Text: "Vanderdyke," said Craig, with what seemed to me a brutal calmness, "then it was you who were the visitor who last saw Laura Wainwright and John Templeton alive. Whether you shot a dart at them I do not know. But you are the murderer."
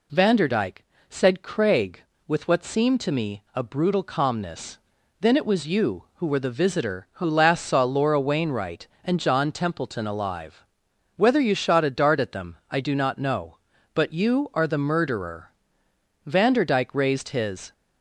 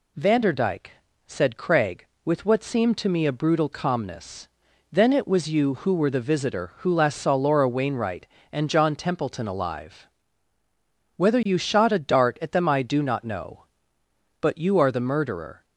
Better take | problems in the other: second | pauses between "them" and "I"; slight; at 12.5 s; 0.16 s long // goes on to say "Vanderdyke raised his"; from 16.2 s on; 1.4 s long

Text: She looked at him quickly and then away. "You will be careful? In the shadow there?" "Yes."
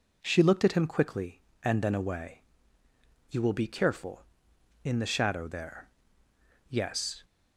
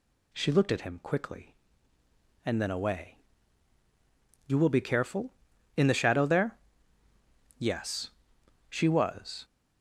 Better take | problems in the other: first | goes on to say "She was"; noticeable; from 8.7 s on; 0.74 s long

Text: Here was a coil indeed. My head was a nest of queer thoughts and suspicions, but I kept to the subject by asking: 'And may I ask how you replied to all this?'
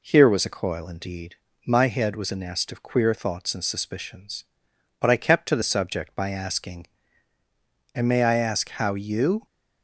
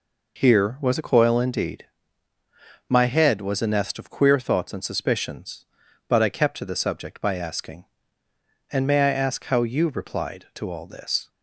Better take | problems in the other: second | stops before "replied to all this"; at 9.4 s

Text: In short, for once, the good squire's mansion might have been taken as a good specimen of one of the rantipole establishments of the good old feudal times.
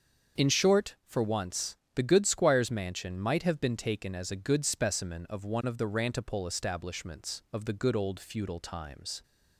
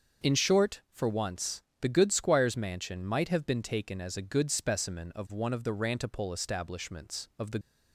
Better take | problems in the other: first | starts louder than the rest; until 1.3 s; 6.5 dB; also in the first // stops before "good old feudal times"; at 7.6 s

